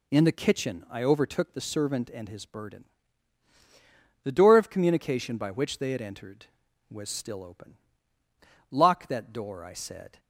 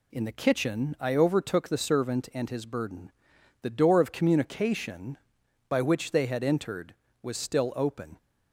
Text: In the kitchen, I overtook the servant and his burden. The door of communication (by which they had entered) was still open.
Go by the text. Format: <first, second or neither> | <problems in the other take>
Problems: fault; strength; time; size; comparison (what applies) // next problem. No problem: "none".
second | goes on to say "Lock that door I said"; from 8.6 s on; 1.5 s long